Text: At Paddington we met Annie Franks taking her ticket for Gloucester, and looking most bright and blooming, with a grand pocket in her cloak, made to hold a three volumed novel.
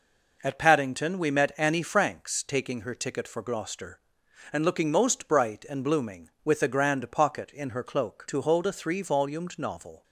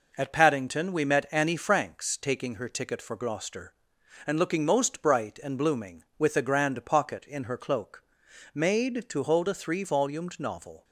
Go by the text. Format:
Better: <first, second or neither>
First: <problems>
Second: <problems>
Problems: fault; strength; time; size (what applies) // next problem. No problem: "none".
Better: second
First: skips "made"; at 8.2 s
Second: none